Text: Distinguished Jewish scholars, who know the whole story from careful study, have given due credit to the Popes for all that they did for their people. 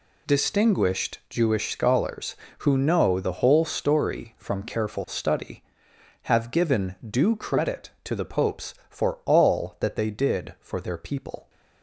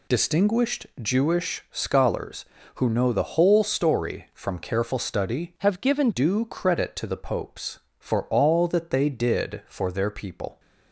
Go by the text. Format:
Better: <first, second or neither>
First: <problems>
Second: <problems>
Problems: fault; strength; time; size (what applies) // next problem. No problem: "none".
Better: first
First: none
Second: pauses between "Distinguished" and "Jewish"; slight; at 0.8 s; 0.16 s long // changes voice from "have" to "given"; from 5.5 to 6.0 s; 0.5 s long